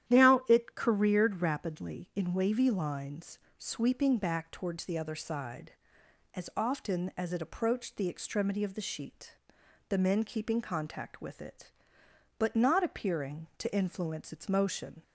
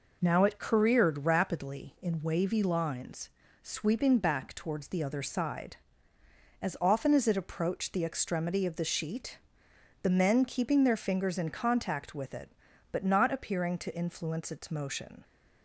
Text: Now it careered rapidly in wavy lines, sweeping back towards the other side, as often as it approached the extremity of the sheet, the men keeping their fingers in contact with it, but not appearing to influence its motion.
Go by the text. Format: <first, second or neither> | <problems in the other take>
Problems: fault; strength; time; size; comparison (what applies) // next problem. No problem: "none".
second | starts louder than the rest; strong; until 1.1 s; 11 dB // skips "their fingers in"; at 10.6 s